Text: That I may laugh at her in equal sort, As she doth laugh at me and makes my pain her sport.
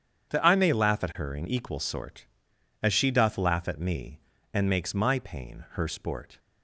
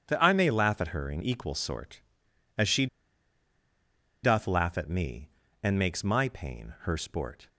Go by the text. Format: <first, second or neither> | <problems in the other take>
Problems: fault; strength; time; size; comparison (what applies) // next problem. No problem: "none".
first | starts louder than the rest; strong; until 1.0 s; 8 dB; strong in the first // pauses between "she" and "doth"; strong; at 2.8 s; 1.3 s long